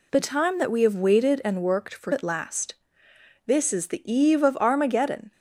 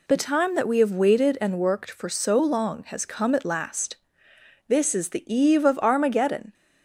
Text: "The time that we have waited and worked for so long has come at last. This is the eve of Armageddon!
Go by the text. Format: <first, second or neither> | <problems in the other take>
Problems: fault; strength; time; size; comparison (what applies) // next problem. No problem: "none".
second | skips "so long has come"; at 2.1 s